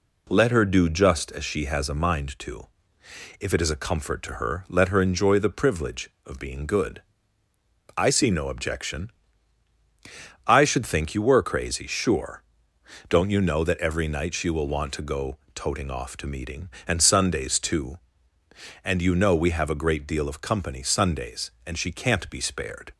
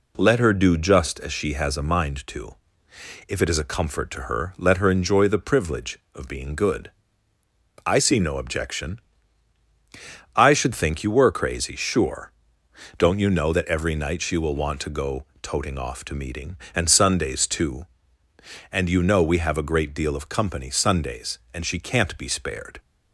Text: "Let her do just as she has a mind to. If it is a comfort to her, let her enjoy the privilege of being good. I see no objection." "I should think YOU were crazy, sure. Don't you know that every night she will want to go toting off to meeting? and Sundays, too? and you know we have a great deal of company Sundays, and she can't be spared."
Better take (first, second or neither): neither